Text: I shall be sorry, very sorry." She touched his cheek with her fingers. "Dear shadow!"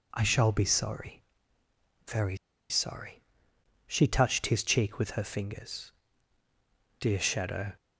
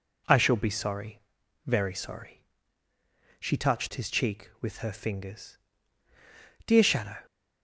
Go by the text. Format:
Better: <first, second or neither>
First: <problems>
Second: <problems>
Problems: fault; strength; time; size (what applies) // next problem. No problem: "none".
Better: second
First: pauses between "very" and "sorry"; slight; at 2.3 s; 0.33 s long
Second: none